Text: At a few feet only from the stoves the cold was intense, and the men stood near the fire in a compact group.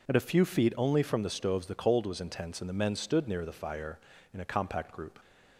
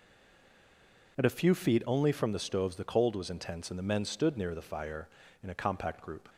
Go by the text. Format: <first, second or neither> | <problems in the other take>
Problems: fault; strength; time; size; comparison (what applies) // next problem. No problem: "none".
first | stays silent before the first word; until 1.1 s; 1.1 s long